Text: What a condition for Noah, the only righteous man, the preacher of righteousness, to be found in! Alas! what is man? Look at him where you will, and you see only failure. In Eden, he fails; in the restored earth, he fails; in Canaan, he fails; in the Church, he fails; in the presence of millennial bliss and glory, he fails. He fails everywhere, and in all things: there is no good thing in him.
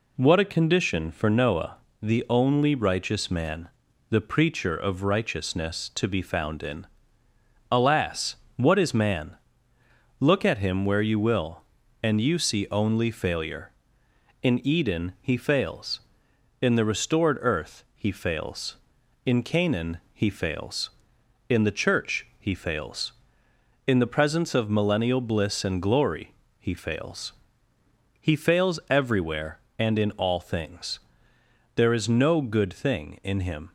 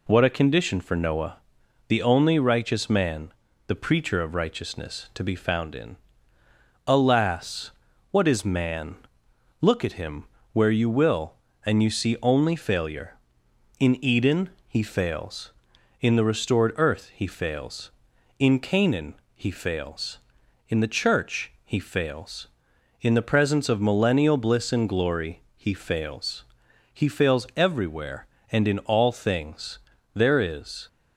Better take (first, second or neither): first